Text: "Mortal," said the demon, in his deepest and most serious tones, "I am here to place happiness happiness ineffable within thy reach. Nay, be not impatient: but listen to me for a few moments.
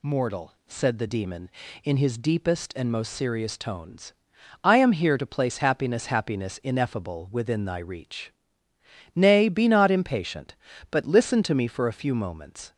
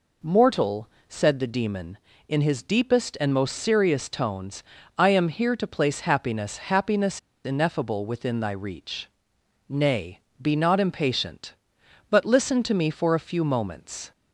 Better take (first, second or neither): first